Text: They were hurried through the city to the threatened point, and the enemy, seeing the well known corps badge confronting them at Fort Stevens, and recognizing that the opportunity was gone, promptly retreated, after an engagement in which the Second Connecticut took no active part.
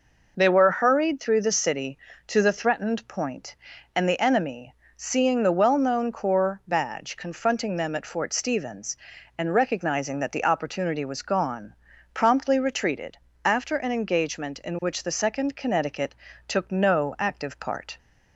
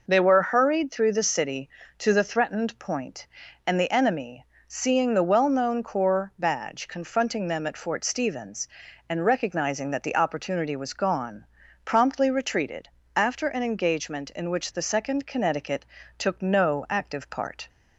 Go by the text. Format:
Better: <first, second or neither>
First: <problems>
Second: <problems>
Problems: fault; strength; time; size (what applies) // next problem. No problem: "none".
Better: neither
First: pauses between "Connecticut" and "took"; slight; at 16.1 s; 0.32 s long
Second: pauses between "Connecticut" and "took"; slight; at 15.8 s; 0.32 s long